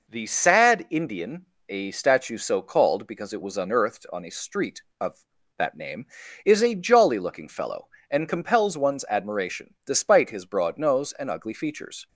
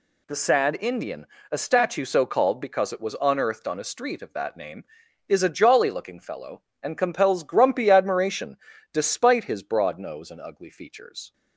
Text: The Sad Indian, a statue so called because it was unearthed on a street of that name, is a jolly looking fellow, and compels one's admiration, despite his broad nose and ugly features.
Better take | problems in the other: first | says "grumpy" for "one's"; at 7.4 s

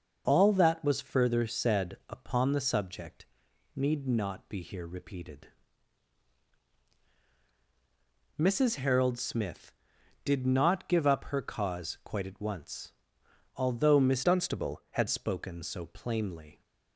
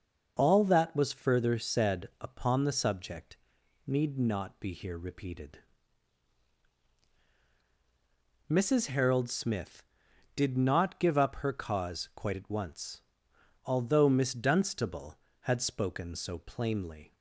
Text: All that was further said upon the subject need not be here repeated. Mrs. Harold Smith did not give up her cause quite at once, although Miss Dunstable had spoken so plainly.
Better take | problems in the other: second | starts louder than the rest; noticeable; until 1.2 s; 6 dB; noticeable in the second // pauses between "subject" and "need"; noticeable; at 3.2 s; 0.50 s long; noticeable in the second // changes voice from "Dunstable" to "had"; from 14.2 to 15.0 s; 0.8 s long

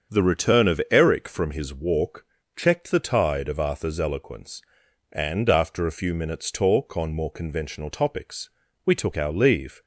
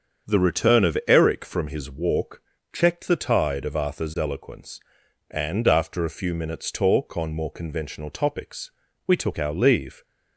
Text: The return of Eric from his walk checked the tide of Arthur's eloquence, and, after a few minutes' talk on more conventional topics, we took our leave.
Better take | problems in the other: neither | starts louder than the rest; strong; the same in both // pauses between "walk" and "checked"; slight; the same in both

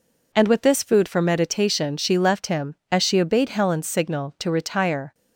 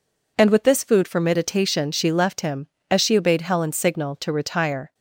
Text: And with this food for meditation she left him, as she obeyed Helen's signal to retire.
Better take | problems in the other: neither | none

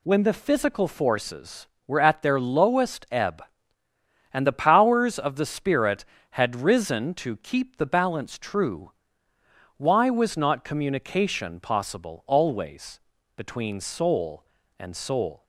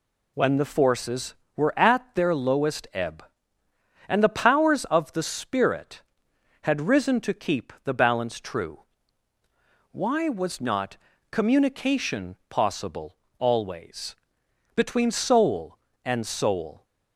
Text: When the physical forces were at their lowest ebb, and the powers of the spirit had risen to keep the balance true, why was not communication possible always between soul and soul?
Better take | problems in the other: first | skips "physical"; at 0.6 s // pauses between "not" and "communication"; slight; at 10.9 s; 0.34 s long // pauses between "communication" and "possible"; slight; at 12.3 s; 0.16 s long // pauses between "possible" and "always"; slight; at 13.1 s; 0.22 s long // pauses between "always" and "between"; noticeable; at 14.1 s; 0.60 s long; also in the first

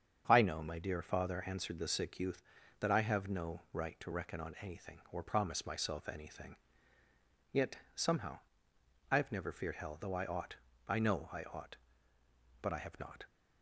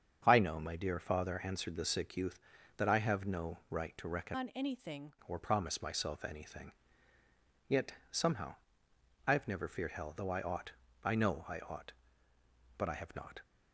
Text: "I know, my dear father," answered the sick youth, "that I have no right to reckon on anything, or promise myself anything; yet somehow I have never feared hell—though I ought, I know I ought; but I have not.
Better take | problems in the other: first | starts louder than the rest; strong; until 1.2 s; 7.5 dB; strong in the first // changes voice from "on" to "anything"; from 4.3 to 5.1 s; 0.8 s long // pauses between "yet" and "somehow"; slight; at 7.9 s; 0.18 s long; slight in the first // pauses between "somehow" and "I"; noticeable; at 8.5 s; 0.72 s long; noticeable in the first

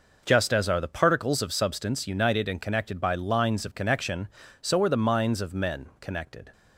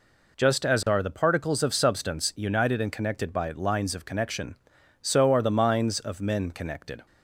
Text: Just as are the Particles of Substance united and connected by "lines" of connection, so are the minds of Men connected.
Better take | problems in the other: neither | none

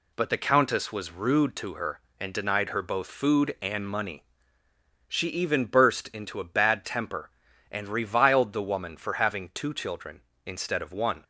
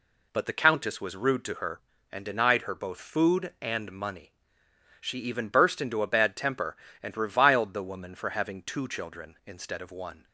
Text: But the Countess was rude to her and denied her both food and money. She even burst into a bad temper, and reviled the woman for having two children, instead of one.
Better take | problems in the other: neither | none

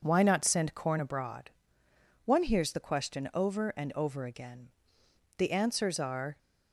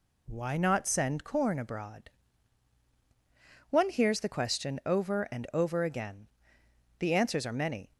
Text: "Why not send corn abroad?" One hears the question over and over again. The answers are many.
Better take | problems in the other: second | stops before "many"; at 6.3 s

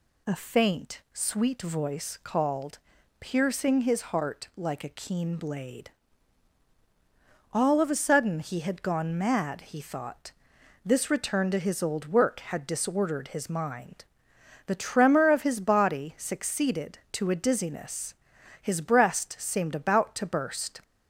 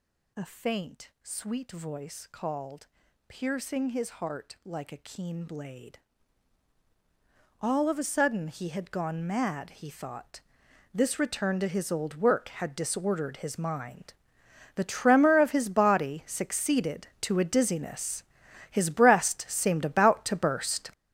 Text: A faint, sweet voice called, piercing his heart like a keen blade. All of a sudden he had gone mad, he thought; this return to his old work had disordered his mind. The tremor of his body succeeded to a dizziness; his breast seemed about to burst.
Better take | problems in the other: first | gets louder; strong; throughout; 11.5 dB

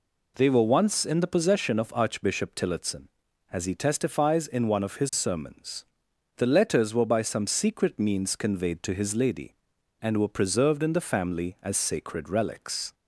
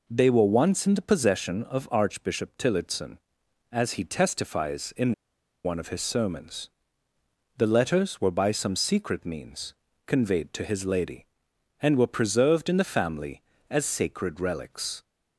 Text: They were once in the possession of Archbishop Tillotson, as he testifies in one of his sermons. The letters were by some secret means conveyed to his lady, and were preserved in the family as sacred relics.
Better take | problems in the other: first | pauses between "in" and "one"; noticeable; at 5.1 s; 0.51 s long // pauses between "means" and "conveyed"; slight; at 9.7 s; 0.34 s long

